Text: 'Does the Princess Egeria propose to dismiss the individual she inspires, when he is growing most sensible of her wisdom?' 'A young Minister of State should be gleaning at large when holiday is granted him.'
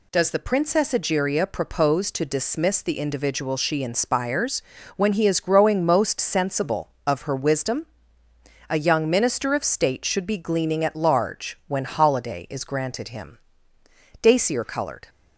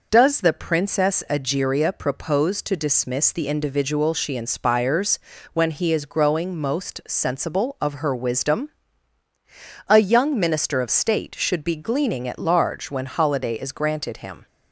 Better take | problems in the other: second | goes on to say "Dacier coloured"; noticeable; from 14.2 s on; 0.86 s long

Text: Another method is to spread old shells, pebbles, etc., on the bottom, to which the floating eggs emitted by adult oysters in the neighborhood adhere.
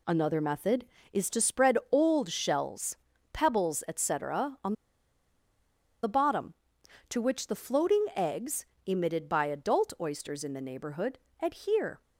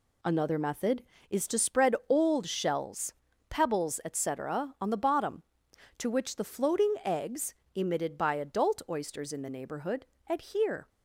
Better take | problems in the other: second | pauses between "on" and "the"; strong; at 4.7 s; 1.2 s long // pauses between "eggs" and "emitted"; slight; at 8.6 s; 0.20 s long; slight in the second // pauses between "neighborhood" and "adhere"; slight; at 11.1 s; 0.24 s long; slight in the second

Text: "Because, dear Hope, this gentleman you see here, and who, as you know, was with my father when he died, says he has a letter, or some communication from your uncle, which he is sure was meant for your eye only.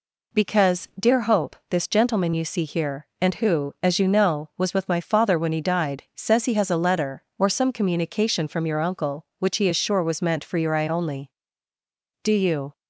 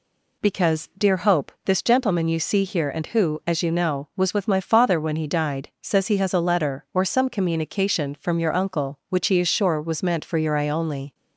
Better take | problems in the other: second | goes on to say "Do you"; from 12.2 s on; 0.54 s long

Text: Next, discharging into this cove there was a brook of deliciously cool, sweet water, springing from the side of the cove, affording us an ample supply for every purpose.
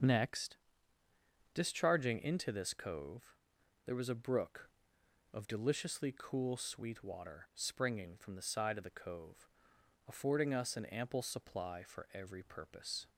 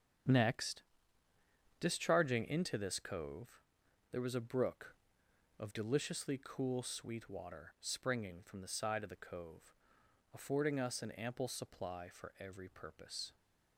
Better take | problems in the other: first | gets quieter; strong; throughout; 8.5 dB // starts louder than the rest; strong; until 2.2 s; 8 dB; also in the first // pauses between "cove" and "there"; noticeable; at 3.6 s; 0.50 s long; noticeable in the first

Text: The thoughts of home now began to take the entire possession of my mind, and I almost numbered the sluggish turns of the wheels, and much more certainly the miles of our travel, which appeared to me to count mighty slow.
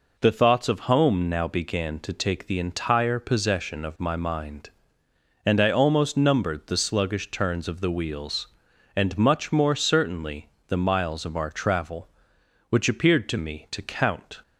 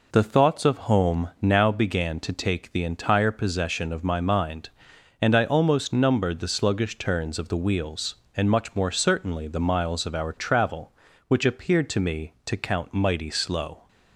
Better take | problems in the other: second | pauses between "certainly" and "the"; slight; at 10.4 s; 0.18 s long // stops before "mighty slow"; at 14.4 s

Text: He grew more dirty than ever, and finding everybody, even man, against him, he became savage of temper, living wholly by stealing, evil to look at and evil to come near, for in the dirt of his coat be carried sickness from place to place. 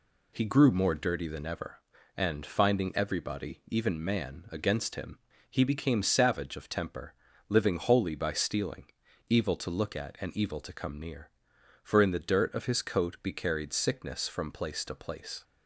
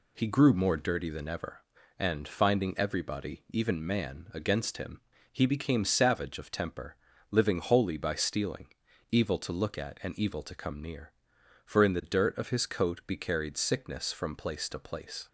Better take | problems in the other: neither | none

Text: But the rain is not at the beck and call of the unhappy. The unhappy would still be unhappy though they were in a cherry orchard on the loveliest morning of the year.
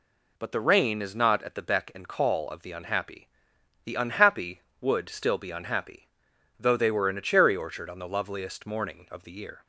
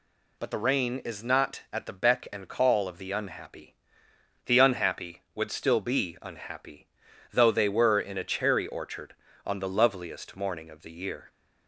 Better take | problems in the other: neither | pauses between "unhappy" and "though"; noticeable; the same in both

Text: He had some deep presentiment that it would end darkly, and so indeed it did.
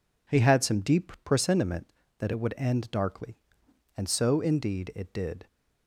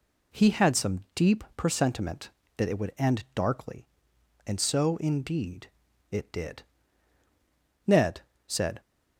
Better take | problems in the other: first | pauses between "indeed" and "it"; at 5.6 s; 0.44 s long // goes on to say "Ned said"; noticeable; from 7.8 s on; 0.94 s long

